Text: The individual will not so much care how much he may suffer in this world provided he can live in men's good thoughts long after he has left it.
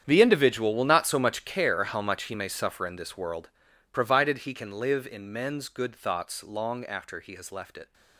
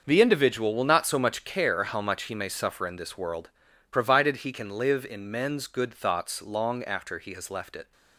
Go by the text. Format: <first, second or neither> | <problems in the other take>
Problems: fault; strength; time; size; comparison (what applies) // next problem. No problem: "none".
second | gets quieter; strong; throughout; 17 dB // starts louder than the rest; strong; until 1.0 s; 8.5 dB; also in the second // pauses between "world" and "provided"; at 3.4 s; 0.44 s long; also in the second